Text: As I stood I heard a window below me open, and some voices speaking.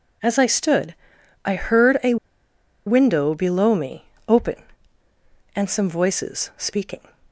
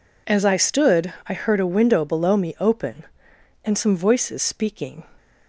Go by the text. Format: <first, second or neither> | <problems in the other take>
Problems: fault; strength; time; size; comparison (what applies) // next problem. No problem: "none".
second | pauses between "stood" and "I"; noticeable; at 0.9 s; 0.50 s long // pauses between "a" and "window"; noticeable; at 2.1 s; 0.71 s long // pauses between "me" and "open"; slight; at 4.0 s; 0.20 s long